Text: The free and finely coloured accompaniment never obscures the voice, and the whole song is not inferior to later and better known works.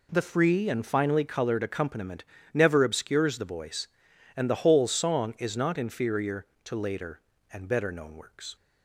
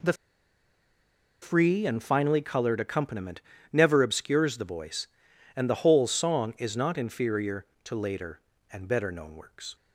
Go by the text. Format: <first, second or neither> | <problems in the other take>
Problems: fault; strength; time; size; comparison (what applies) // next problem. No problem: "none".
first | pauses between "The" and "free"; strong; at 0.1 s; 1.2 s long // pauses between "accompaniment" and "never"; slight; at 3.4 s; 0.32 s long; slight in the first